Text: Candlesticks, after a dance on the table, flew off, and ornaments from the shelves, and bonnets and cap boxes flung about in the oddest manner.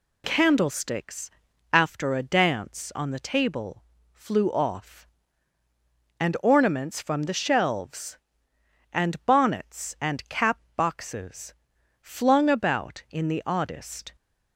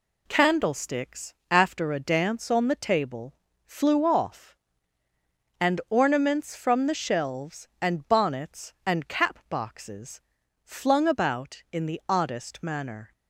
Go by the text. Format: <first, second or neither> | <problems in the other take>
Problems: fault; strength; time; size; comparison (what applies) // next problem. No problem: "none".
second | pauses between "cap" and "boxes"; slight; at 10.5 s; 0.16 s long // pauses between "boxes" and "flung"; noticeable; at 11.5 s; 0.48 s long; also in the second // stops before "manner"; at 14.1 s